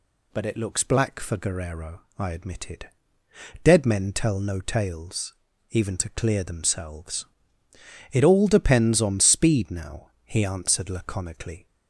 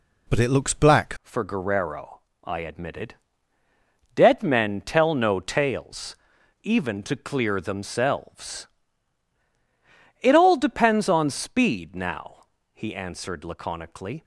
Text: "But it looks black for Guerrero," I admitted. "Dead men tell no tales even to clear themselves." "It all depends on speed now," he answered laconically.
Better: first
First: pauses between "tales" and "even"; at 5.3 s; 0.38 s long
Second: changes voice at "for"; from 1.2 s on; 13.0 s long // pauses between "tales" and "even"; noticeable; at 6.1 s; 0.46 s long

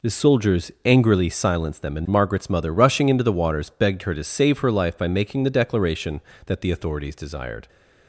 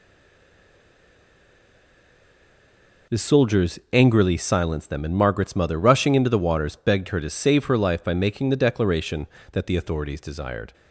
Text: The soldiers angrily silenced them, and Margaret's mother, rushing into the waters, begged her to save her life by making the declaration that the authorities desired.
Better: first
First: none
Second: stays silent before the first word; strong; until 3.0 s; 3.0 s long

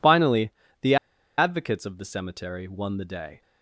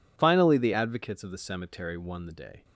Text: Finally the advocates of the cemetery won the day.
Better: second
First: pauses between "Finally" and "the"; slight; at 0.5 s; 0.30 s long // pauses between "the" and "advocates"; at 0.9 s; 0.42 s long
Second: none

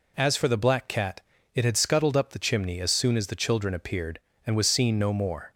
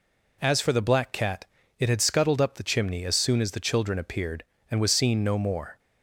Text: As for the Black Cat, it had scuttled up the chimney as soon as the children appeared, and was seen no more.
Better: neither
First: none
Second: none

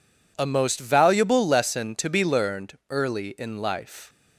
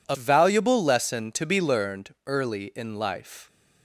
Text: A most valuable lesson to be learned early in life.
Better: first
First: none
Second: skips "most"; at 0.1 s

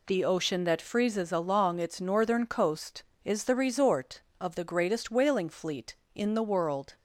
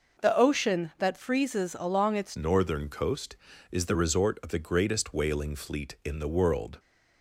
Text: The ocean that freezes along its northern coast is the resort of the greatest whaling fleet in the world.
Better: first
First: none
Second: changes voice at "northern"; from 2.3 s on; 4.4 s long

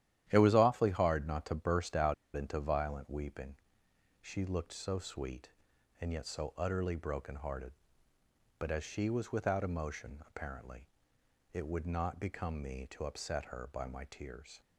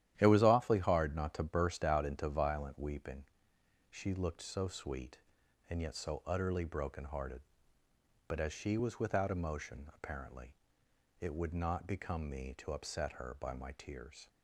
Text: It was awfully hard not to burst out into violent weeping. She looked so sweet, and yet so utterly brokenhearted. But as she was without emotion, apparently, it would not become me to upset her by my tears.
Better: second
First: starts louder than the rest; strong; until 1.2 s; 11.5 dB // pauses between "out" and "into"; slight; at 2.1 s; 0.21 s long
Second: starts louder than the rest; strong; until 1.1 s; 11.5 dB

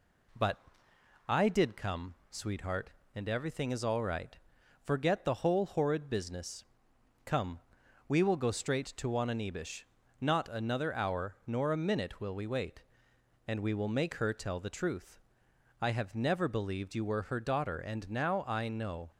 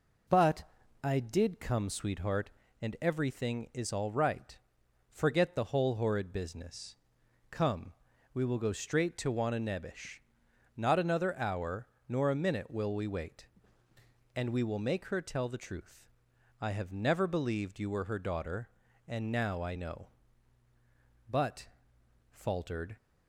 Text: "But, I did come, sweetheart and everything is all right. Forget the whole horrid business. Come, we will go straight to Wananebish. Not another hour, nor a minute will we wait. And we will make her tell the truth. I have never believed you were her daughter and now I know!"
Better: first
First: none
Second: goes on to say "But faltered"; strong; from 21.2 s on; 1.6 s long

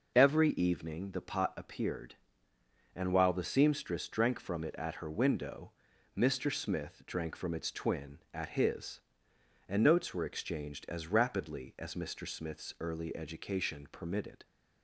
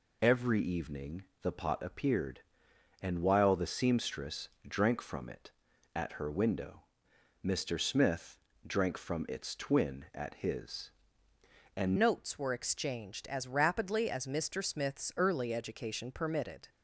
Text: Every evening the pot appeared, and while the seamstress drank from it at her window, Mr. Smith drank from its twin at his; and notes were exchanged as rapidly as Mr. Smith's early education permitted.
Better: first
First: none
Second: pauses between "evening" and "the"; slight; at 1.2 s; 0.18 s long // pauses between "seamstress" and "drank"; slight; at 4.4 s; 0.20 s long // pauses between "Smith" and "drank"; slight; at 8.3 s; 0.30 s long // changes voice at "notes"; from 11.9 s on; 4.7 s long

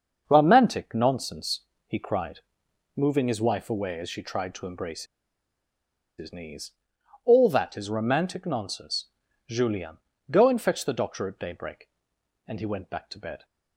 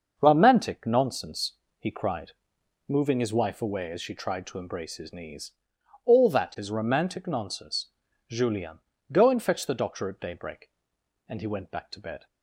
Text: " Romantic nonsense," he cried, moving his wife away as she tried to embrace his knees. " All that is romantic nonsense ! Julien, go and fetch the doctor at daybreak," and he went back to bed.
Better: second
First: starts louder than the rest; until 1.2 s; 6.5 dB // pauses between "embrace" and "his"; at 5.0 s; 1.1 s long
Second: starts louder than the rest; until 1.1 s; 6.5 dB

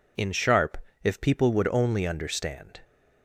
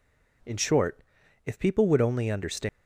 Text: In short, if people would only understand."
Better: second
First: says "sharp" for "short"; at 0.3 s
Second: none

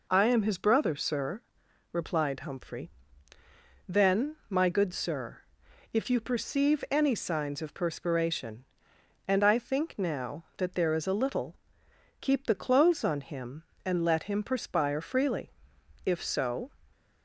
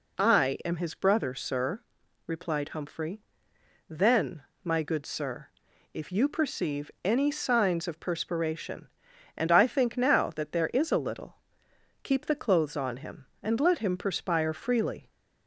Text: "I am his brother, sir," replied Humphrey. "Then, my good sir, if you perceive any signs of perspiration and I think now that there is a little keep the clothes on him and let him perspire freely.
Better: second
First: pauses between "little" and "keep"; noticeable; at 11.5 s; 0.64 s long // goes on to say "If so"; noticeable; from 16.0 s on; 0.64 s long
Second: pauses between "little" and "keep"; noticeable; at 11.3 s; 0.66 s long

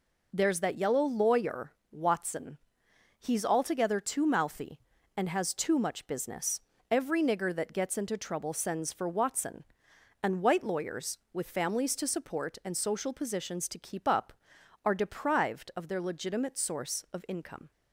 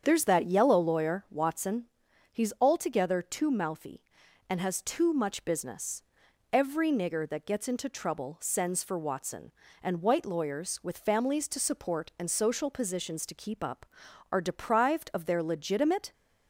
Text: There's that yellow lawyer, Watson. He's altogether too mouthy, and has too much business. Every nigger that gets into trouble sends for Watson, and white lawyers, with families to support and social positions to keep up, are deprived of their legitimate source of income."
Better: first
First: none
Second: starts louder than the rest; strong; until 1.0 s; 7.5 dB // stops before "source of income"; at 16.1 s

